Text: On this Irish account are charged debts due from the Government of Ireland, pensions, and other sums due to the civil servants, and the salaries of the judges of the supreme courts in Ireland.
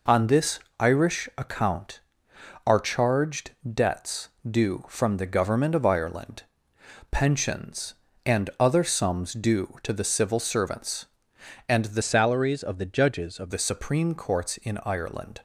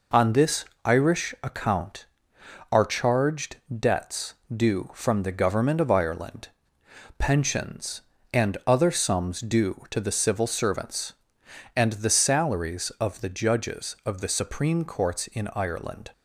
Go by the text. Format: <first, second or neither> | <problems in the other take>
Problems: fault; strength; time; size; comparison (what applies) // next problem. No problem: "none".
second | pauses between "this" and "Irish"; slight; at 0.6 s; 0.18 s long; slight in the second // pauses between "charged" and "debts"; slight; at 3.5 s; 0.18 s long; slight in the second // pauses between "debts" and "due"; slight; at 4.2 s; 0.20 s long; slight in the second // changes voice from "salaries" to "of"; from 12.0 to 13.5 s; 1.5 s long